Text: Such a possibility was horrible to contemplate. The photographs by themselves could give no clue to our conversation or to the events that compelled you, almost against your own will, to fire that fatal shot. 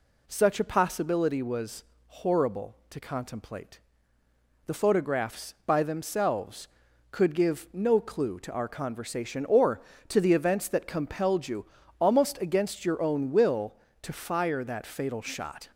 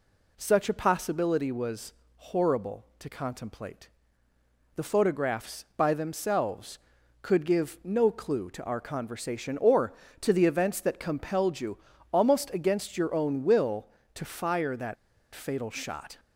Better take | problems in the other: first | pauses between "was" and "horrible"; slight; at 1.9 s; 0.24 s long; slight in the first // pauses between "that" and "fatal"; at 14.9 s; 0.39 s long

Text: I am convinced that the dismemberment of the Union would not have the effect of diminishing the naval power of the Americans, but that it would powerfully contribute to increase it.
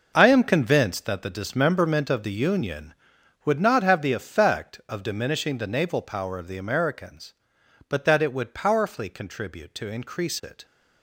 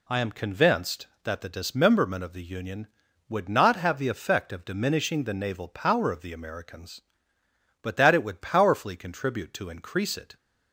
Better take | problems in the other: second | gets quieter; strong; throughout; 11.5 dB

